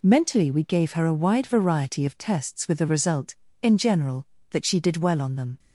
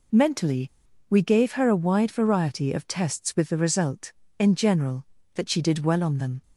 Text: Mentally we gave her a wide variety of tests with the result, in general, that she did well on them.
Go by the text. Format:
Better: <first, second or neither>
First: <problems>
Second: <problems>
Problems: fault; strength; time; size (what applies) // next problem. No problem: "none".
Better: first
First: none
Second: pauses between "Mentally" and "we"; at 0.6 s; 0.41 s long